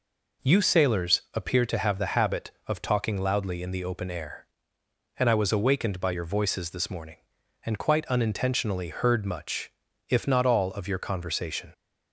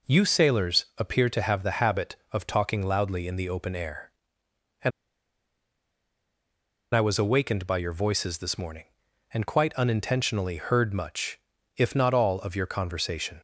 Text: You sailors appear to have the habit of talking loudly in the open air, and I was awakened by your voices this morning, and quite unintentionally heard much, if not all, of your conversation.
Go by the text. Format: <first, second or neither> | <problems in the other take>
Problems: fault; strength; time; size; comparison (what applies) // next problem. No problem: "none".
first | pauses between "and" and "I"; strong; at 4.9 s; 2.0 s long